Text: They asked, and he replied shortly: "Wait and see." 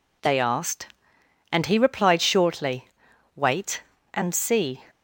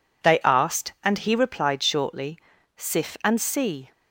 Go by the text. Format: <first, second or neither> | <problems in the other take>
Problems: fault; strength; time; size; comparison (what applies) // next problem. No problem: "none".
first | says "Sif" for "Wait"; at 2.7 s